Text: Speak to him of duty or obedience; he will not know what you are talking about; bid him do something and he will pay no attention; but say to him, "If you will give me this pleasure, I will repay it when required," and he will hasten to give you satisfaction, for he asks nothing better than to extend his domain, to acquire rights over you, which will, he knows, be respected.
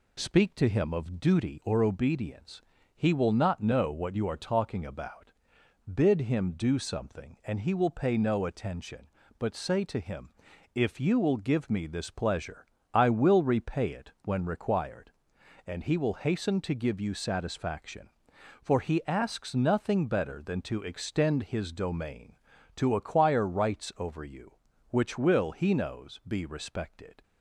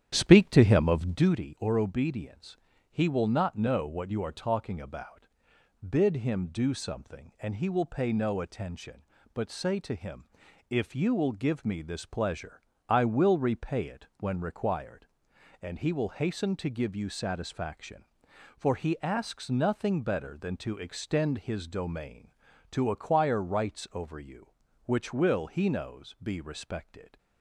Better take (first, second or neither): first